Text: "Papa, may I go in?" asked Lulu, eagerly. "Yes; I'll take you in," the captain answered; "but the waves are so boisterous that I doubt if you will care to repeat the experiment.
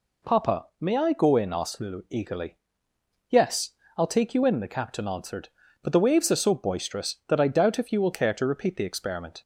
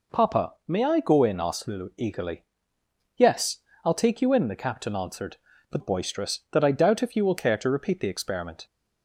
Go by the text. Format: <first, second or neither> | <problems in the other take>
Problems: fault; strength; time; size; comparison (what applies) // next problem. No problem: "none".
first | skips "the waves are so"; at 5.7 s